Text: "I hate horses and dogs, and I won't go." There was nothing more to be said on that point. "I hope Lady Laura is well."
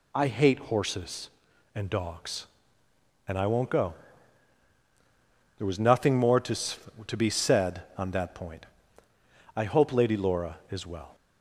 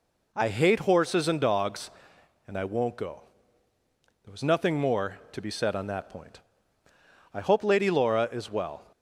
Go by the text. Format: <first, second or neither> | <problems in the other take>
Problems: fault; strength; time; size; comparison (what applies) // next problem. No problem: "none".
second | says "to" twice; at 7.0 s